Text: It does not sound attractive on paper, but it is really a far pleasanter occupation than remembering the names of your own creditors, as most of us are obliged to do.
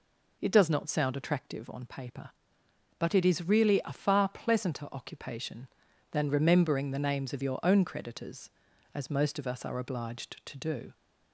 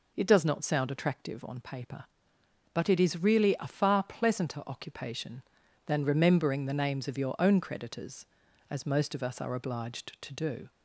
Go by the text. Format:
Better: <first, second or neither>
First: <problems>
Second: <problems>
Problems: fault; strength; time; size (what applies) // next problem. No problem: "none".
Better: neither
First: none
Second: none